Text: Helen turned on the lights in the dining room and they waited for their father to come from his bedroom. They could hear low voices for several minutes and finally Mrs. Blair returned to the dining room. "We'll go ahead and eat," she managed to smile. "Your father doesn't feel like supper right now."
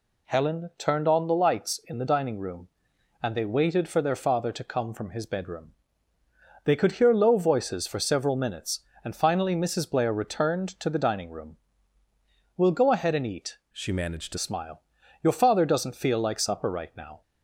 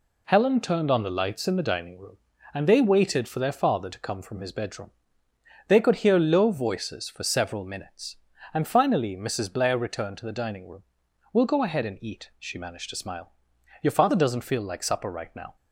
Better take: second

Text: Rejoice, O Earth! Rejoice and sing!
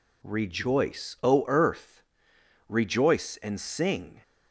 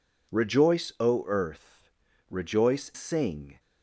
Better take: first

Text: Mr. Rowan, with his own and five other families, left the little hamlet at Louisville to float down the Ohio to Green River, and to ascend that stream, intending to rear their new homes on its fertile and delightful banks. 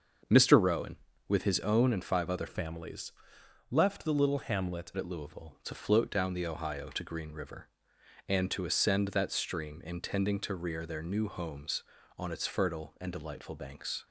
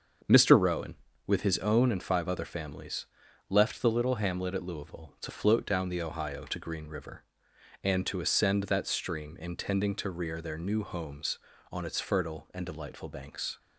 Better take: second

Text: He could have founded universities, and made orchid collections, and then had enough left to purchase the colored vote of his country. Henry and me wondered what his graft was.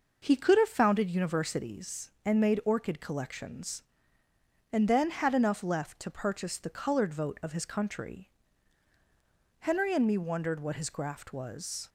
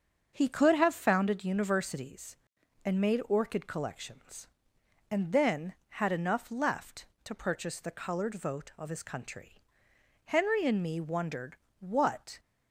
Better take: first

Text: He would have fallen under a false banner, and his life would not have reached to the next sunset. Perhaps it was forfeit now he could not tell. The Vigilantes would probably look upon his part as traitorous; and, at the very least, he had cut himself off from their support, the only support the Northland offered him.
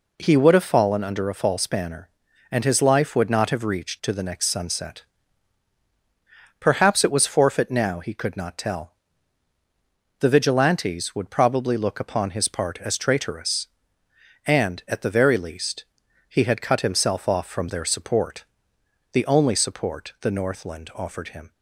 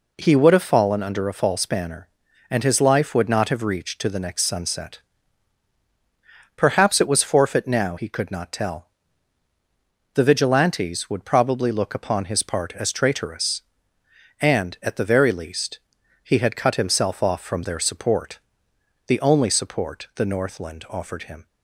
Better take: neither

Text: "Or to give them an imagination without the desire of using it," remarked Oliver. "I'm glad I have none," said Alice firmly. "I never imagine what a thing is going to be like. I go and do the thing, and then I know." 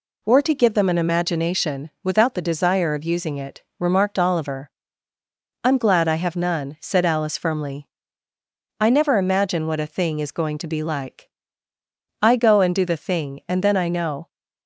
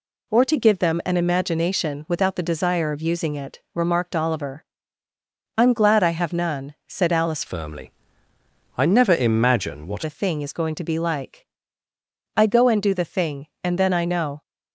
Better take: first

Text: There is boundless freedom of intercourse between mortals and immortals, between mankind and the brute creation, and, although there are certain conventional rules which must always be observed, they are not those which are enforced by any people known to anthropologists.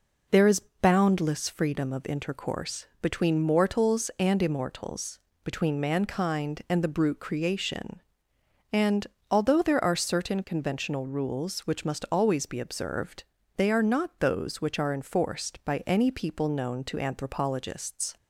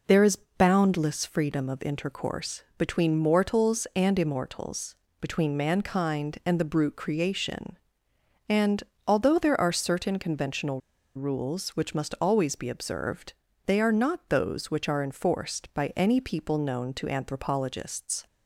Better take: first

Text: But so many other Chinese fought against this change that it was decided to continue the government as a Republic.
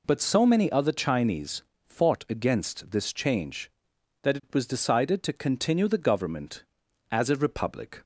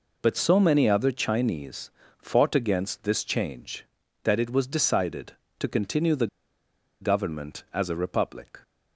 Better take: first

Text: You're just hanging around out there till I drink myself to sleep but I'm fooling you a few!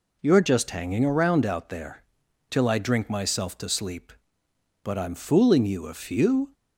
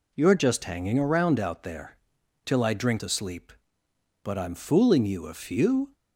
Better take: first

